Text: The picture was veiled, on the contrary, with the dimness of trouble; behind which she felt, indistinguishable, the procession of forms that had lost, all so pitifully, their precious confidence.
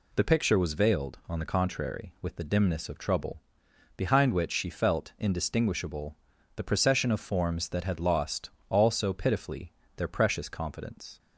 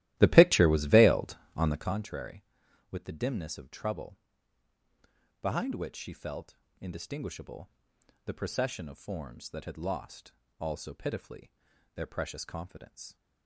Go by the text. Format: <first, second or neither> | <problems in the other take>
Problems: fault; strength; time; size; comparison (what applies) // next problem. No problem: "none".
first | starts louder than the rest; strong; until 2.0 s; 15 dB